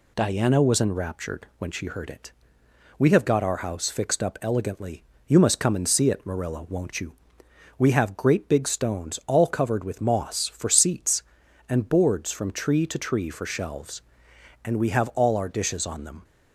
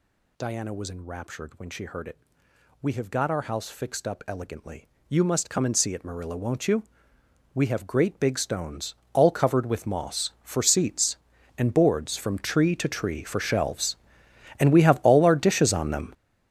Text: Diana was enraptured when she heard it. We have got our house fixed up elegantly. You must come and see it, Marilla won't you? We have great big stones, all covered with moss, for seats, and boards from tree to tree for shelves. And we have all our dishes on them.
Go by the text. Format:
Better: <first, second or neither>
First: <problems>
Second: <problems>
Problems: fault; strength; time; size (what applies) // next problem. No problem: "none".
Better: first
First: none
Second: gets louder; strong; throughout; 13.5 dB